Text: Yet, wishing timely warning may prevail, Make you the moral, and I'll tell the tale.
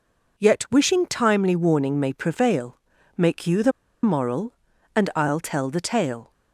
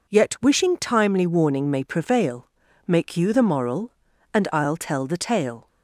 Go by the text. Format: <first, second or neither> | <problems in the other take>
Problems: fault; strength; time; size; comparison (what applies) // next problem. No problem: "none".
second | pauses between "the" and "moral"; slight; at 3.7 s; 0.32 s long